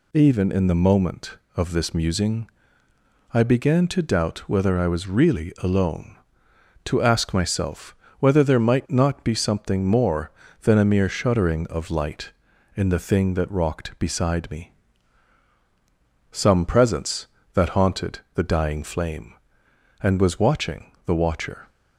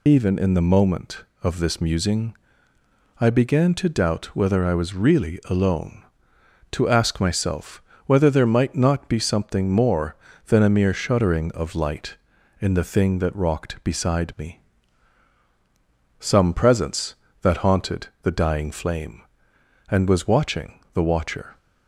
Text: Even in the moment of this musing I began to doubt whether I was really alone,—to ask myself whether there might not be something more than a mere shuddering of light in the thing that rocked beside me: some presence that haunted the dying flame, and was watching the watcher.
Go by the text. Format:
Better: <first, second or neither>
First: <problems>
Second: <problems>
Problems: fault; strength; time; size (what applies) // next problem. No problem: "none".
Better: first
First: pauses between "musing" and "I"; noticeable; at 2.4 s; 0.84 s long // pauses between "myself" and "whether"; slight; at 7.9 s; 0.24 s long // pauses between "haunted" and "the"; slight; at 18.1 s; 0.16 s long // pauses between "watching" and "the"; slight; at 20.9 s; 0.16 s long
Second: loses the start of "Even"; at 0.0 s; 65 ms // pauses between "musing" and "I"; noticeable; at 2.3 s; 0.84 s long // pauses between "myself" and "whether"; slight; at 7.8 s; 0.24 s long // pauses between "haunted" and "the"; slight; at 18.0 s; 0.16 s long // pauses between "watching" and "the"; slight; at 20.7 s; 0.16 s long